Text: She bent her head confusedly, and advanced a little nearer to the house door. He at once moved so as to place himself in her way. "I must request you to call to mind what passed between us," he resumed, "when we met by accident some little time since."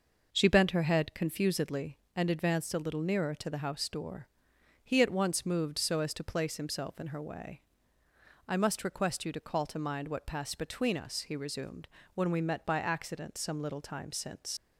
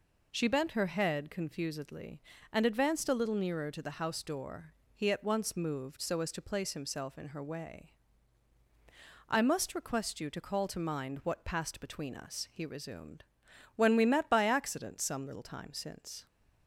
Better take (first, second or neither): second